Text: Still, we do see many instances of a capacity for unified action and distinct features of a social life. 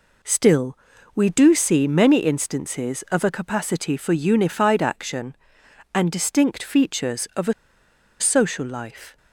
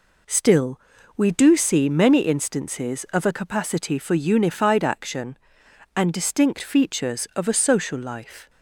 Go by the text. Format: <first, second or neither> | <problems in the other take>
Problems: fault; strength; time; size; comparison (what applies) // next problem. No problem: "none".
second | pauses between "a" and "social"; noticeable; at 7.5 s; 0.67 s long